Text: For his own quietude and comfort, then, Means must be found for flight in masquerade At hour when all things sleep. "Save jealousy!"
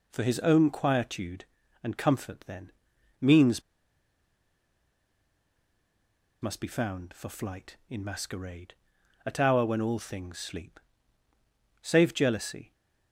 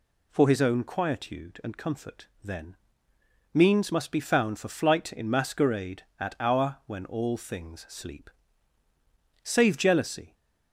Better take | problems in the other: second | pauses between "Means" and "must"; strong; at 3.6 s; 2.7 s long

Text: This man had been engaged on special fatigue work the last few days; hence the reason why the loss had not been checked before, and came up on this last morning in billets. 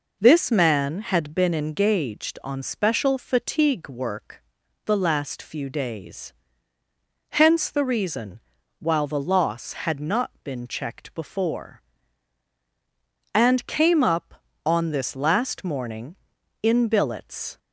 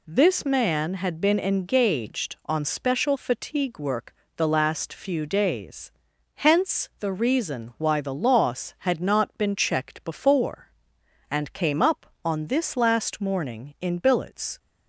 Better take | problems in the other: second | pauses between "work" and "the"; at 4.4 s; 0.44 s long; slight in the second // says "while" for "why"; at 8.7 s

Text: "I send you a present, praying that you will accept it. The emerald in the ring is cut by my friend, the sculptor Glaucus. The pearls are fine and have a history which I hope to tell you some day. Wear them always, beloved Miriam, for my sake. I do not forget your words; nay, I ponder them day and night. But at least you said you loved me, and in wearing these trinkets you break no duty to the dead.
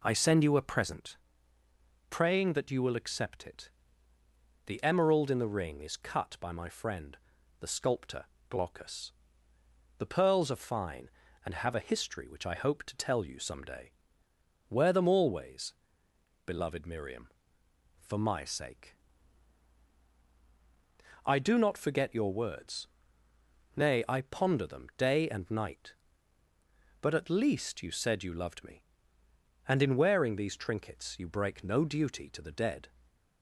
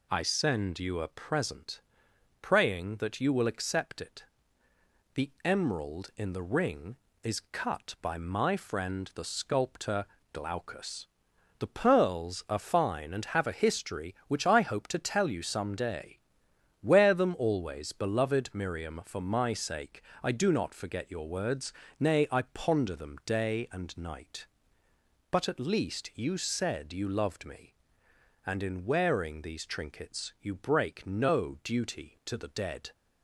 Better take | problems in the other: neither | pauses between "sculptor" and "Glaucus"; slight; the same in both

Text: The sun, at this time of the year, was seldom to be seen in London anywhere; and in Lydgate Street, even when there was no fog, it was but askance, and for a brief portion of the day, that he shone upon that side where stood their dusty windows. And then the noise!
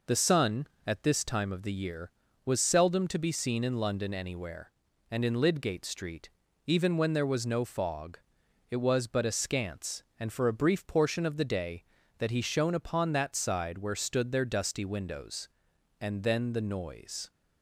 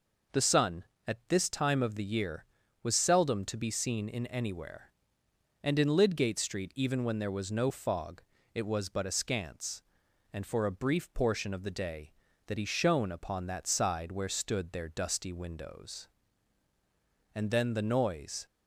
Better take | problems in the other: first | skips "London"; at 4.2 s

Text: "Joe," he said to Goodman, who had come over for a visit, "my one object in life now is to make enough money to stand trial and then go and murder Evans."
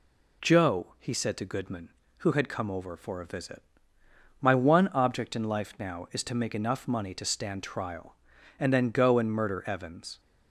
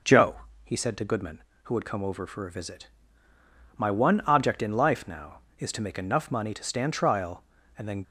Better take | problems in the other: first | stops before "go and murder Evans"; at 8.0 s

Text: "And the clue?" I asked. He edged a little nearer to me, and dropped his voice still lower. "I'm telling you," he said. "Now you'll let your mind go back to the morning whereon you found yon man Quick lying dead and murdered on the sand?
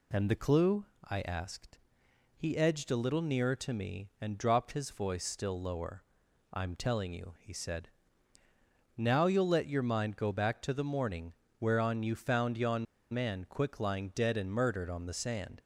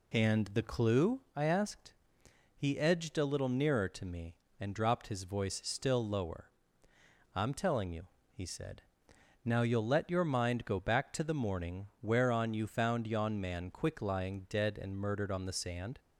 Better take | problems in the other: second | pauses between "morning" and "whereon"; slight; at 11.3 s; 0.28 s long // pauses between "yon" and "man"; slight; at 12.8 s; 0.28 s long

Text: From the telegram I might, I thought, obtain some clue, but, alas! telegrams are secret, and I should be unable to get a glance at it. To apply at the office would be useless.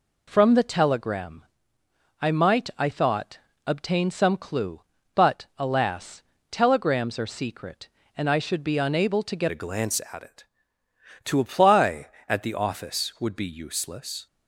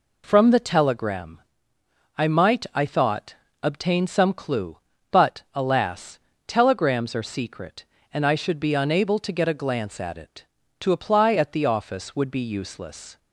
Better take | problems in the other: second | pauses between "telegram" and "I"; noticeable; at 1.4 s; 0.74 s long; noticeable in the second // changes voice at "a"; from 9.5 s on; 4.7 s long

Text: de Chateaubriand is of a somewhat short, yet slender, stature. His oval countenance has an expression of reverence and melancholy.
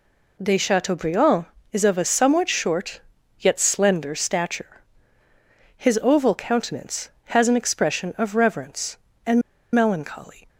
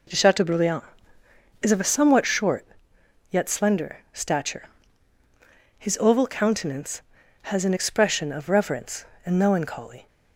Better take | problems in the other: second | pauses between "and" and "melancholy"; slight; at 9.4 s; 0.32 s long

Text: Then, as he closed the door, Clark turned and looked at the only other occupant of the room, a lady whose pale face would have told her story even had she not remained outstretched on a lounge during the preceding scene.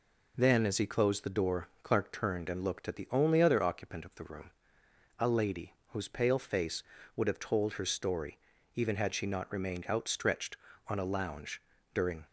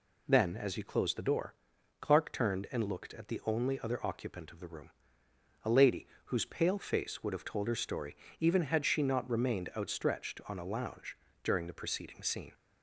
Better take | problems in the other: second | pauses between "lady" and "whose"; slight; at 5.7 s; 0.20 s long; slight in the second // pauses between "story" and "even"; at 8.3 s; 0.38 s long; slight in the second // pauses between "lounge" and "during"; slight; at 11.6 s; 0.32 s long; slight in the second // stops before "the preceding scene"; at 12.2 s

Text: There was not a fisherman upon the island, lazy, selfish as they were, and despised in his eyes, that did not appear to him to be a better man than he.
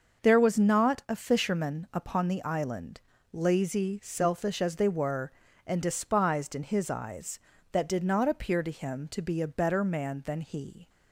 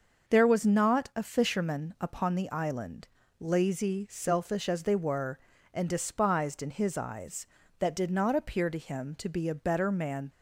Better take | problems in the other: first | starts louder than the rest; until 1.3 s; 6 dB; also in the first // stops before "than he"; at 10.3 s

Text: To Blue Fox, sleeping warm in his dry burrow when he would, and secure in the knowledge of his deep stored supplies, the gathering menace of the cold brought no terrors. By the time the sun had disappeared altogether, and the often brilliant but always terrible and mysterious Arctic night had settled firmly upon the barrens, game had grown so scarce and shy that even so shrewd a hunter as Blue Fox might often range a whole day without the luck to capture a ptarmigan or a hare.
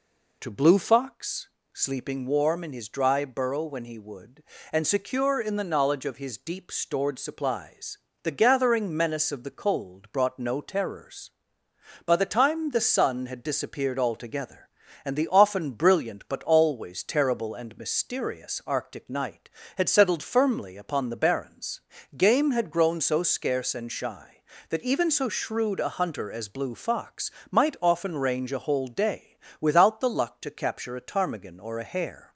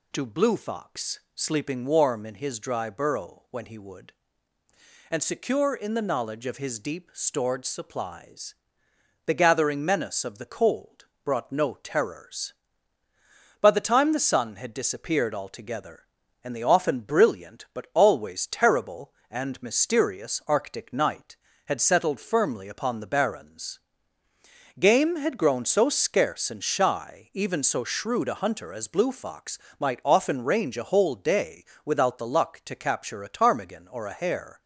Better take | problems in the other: first | pauses between "cold" and "brought"; slight; at 11.0 s; 0.18 s long // skips "that"; at 27.3 s // pauses between "Fox" and "might"; slight; at 29.5 s; 0.20 s long; slight in the first // pauses between "day" and "without"; slight; at 31.6 s; 0.18 s long; slight in the first

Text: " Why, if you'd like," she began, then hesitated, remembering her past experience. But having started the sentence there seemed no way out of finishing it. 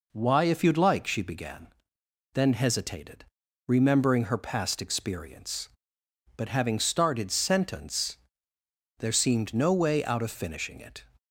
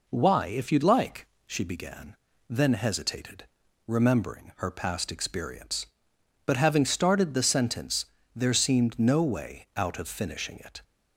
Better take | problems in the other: second | skips "the"; at 7.3 s // pauses between "sentence" and "there"; noticeable; at 8.1 s; 0.82 s long; slight in the second

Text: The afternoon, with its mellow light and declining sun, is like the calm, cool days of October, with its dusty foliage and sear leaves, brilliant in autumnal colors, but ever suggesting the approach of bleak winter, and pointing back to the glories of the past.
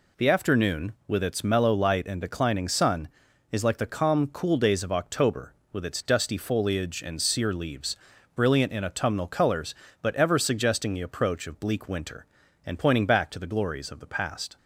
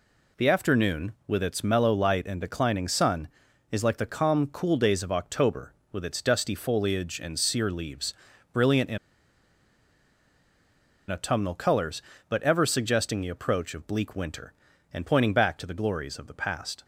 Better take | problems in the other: first | pauses between "in" and "autumnal"; strong; at 8.9 s; 2.1 s long

